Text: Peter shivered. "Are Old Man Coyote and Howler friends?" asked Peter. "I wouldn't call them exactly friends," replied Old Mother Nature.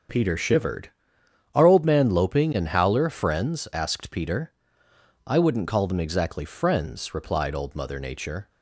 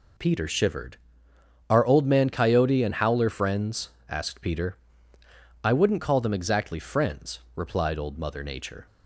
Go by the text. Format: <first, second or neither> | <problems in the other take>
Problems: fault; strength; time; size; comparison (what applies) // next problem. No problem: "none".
second | starts louder than the rest; strong; until 1.7 s; 7 dB // says "Loping" for "Coyote"; at 2.1 s